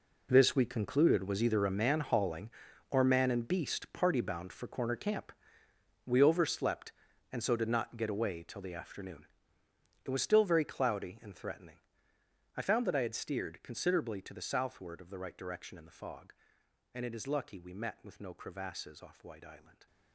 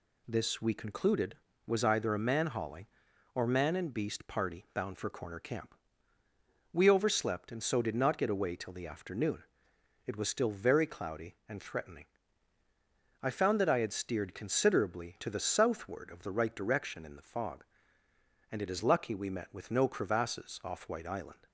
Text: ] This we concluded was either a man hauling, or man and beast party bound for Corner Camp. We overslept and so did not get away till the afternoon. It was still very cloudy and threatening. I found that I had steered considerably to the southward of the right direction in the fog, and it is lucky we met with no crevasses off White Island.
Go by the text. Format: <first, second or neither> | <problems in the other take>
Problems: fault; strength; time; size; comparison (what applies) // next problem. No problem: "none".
second | gets quieter; strong; throughout; 14 dB